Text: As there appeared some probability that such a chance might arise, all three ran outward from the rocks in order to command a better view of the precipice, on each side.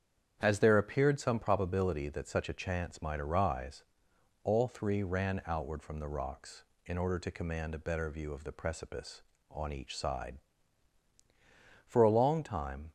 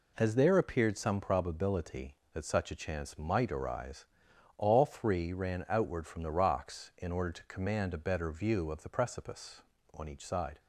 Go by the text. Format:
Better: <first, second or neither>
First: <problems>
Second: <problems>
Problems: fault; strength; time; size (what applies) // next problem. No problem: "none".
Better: second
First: starts louder than the rest; strong; until 1.4 s; 8.5 dB // goes on to say "For a long time"; noticeable; from 11.8 s on; 1.0 s long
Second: none